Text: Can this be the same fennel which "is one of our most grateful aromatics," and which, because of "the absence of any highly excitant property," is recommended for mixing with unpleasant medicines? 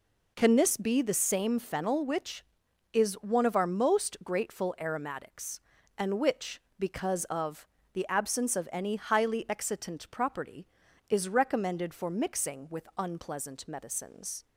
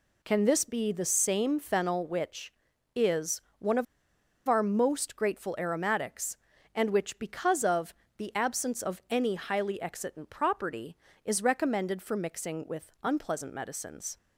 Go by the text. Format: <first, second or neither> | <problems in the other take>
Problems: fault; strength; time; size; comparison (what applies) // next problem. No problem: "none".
first | pauses between "is" and "one"; slight; at 3.4 s; 0.16 s long // pauses between "of" and "our"; noticeable; at 3.8 s; 0.63 s long // pauses between "of" and "the"; slight; at 7.9 s; 0.22 s long; slight in the first